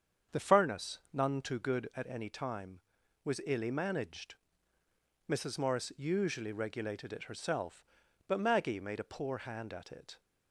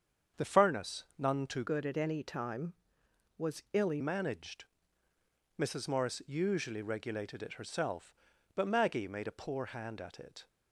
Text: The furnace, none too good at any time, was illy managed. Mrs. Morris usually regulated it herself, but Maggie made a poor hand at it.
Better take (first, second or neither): first